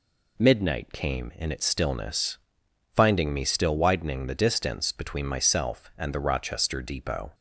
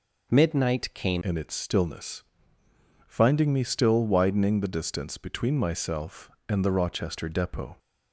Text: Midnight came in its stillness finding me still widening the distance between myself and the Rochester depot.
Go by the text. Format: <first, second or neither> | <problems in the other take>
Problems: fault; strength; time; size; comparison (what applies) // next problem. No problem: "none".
first | changes voice at "in"; from 1.2 s on; 6.5 s long // pauses between "stillness" and "finding"; noticeable; at 2.2 s; 0.86 s long; noticeable in the first